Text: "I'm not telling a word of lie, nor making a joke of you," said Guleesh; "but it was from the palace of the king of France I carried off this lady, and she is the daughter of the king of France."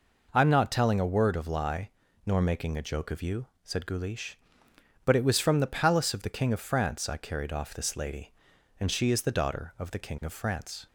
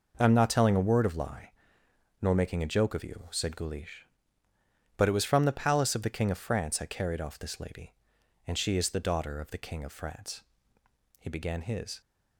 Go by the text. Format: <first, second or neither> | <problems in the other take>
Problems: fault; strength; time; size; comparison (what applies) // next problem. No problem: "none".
first | goes on to say "He began his"; noticeable; from 11.1 s on; 0.82 s long